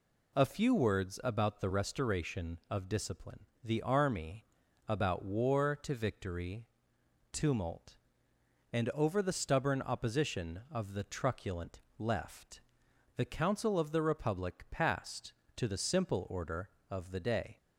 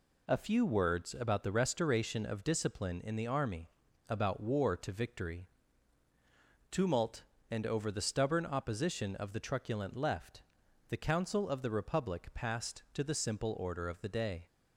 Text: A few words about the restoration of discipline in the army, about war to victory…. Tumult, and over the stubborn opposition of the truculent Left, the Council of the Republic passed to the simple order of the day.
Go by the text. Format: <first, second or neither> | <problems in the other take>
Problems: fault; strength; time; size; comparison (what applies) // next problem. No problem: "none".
second | skips "in"; at 3.5 s // pauses between "truculent" and "Left"; slight; at 11.7 s; 0.18 s long